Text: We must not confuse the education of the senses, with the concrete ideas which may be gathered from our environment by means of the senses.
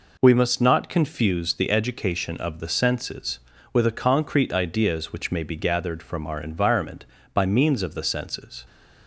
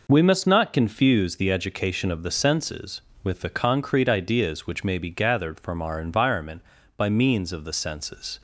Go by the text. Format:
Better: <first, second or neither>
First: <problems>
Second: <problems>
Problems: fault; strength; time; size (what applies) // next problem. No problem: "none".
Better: neither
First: none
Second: none